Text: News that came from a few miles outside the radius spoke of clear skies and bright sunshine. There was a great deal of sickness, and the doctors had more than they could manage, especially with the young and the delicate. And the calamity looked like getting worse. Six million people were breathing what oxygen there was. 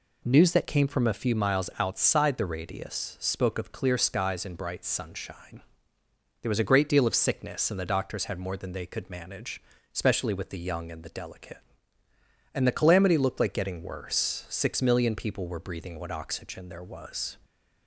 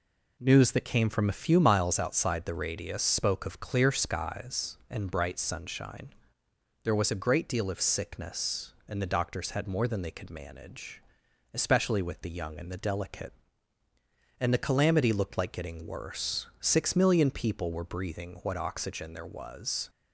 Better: neither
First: none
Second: none

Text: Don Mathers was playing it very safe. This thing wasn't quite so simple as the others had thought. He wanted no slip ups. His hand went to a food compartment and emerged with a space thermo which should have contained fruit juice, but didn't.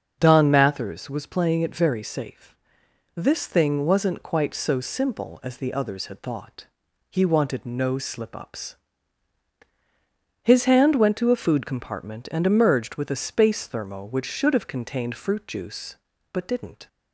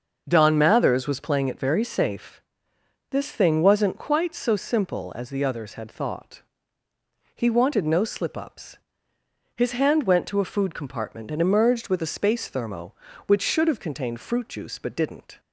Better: neither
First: starts louder than the rest; until 1.2 s; 6.5 dB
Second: starts louder than the rest; until 1.2 s; 6 dB

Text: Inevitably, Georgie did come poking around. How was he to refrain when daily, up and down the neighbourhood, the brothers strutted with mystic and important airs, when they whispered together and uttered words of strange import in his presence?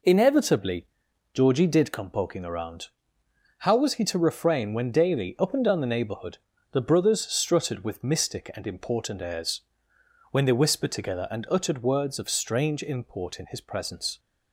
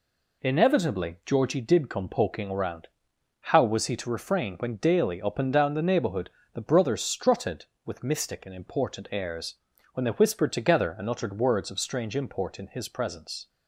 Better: neither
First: none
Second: none

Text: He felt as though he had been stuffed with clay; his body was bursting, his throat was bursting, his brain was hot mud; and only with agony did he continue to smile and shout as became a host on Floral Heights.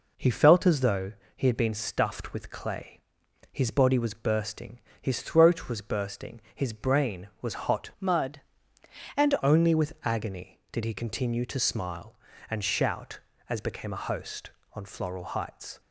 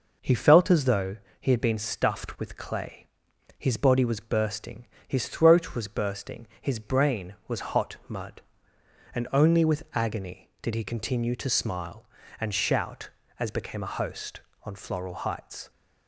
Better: second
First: pauses between "though" and "he"; slight; at 1.1 s; 0.24 s long // changes voice from "mud" to "and"; from 7.9 to 9.3 s; 1.4 s long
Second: pauses between "though" and "he"; slight; at 1.1 s; 0.24 s long

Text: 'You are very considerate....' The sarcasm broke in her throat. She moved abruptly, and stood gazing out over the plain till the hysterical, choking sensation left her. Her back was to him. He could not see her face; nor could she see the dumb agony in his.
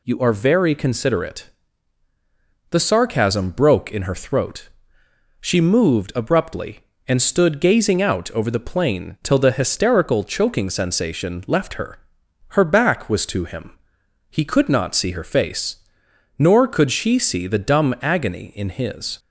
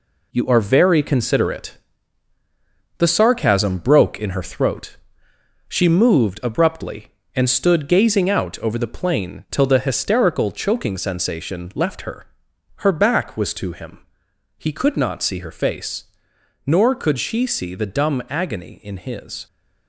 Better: first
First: none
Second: gets quieter; throughout; 6.5 dB

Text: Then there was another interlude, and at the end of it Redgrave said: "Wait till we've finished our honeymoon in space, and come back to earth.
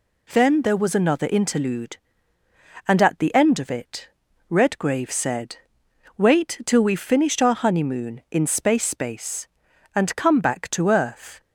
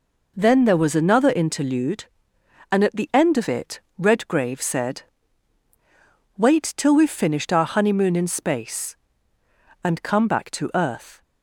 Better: second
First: pauses between "it" and "Redgrave"; at 4.0 s; 0.42 s long // says "space" twice; at 8.8 s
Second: pauses between "it" and "Redgrave"; slight; at 3.7 s; 0.18 s long

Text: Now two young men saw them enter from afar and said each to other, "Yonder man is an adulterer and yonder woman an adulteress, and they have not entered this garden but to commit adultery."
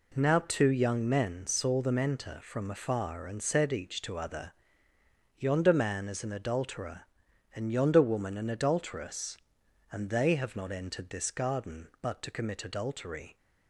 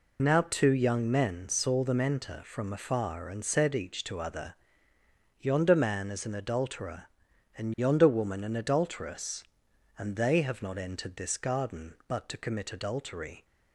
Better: first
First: none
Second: loses the start of "Now"; at 0.1 s; 60 ms

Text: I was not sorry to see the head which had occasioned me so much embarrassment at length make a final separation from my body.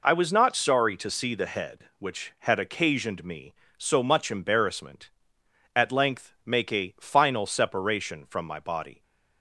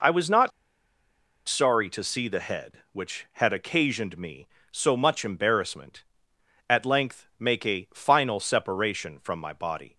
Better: first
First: none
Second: pauses between "not" and "sorry"; noticeable; at 0.5 s; 0.96 s long

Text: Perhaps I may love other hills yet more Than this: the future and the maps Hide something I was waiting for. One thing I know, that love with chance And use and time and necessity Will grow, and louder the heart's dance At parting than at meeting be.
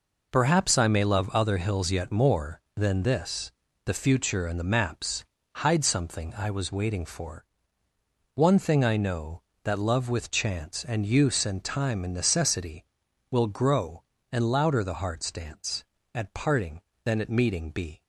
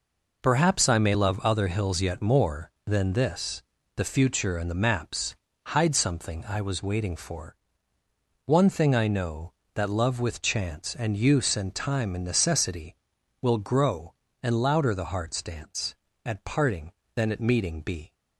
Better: neither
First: pauses between "maps" and "Hide"; slight; at 5.2 s; 0.30 s long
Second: pauses between "maps" and "Hide"; slight; at 5.3 s; 0.30 s long

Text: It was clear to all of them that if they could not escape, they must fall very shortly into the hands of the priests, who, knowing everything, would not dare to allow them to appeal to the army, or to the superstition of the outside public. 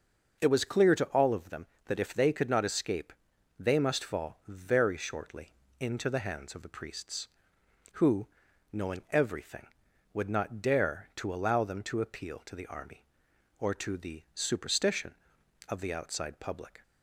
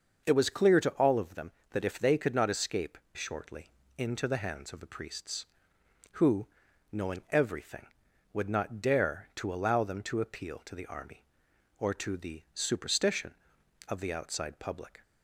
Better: first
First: starts louder than the rest; noticeable; until 1.4 s; 6 dB // pauses between "shortly" and "into"; slight; at 5.5 s; 0.28 s long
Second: starts louder than the rest; until 1.2 s; 6.5 dB // skips "they must fall very"; at 3.0 s // pauses between "shortly" and "into"; slight; at 3.6 s; 0.28 s long

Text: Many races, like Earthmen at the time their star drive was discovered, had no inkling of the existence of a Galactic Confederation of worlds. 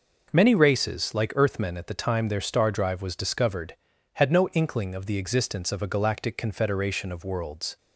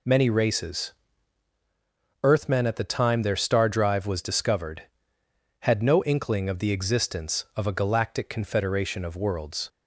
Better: first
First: none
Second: skips "like"; at 1.5 s

